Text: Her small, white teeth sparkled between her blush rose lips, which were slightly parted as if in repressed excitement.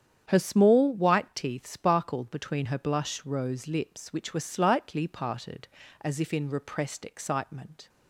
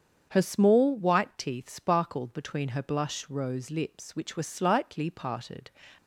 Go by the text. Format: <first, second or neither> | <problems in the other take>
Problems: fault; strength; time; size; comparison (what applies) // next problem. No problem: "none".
first | starts louder than the rest; strong; until 1.3 s; 7.5 dB; strong in the first // stops before "as if in repressed excitement"; at 5.9 s